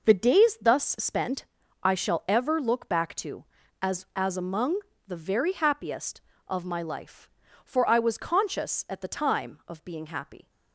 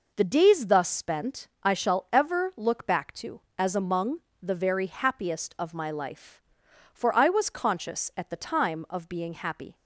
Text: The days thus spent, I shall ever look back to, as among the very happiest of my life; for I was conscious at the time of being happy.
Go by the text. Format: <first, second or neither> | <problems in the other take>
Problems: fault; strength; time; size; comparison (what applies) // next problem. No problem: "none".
second | says "as" twice; at 4.1 s // pauses between "among" and "the"; slight; at 4.7 s; 0.28 s long; slight in the second